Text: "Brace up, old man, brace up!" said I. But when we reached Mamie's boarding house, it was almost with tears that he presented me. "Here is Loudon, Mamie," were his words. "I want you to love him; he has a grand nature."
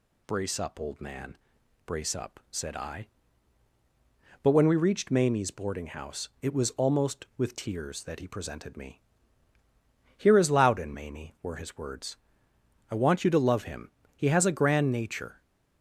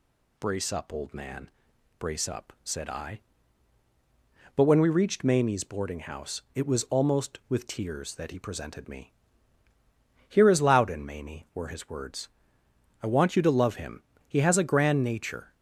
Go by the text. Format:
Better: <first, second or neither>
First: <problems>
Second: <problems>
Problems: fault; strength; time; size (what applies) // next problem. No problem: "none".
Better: neither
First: none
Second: none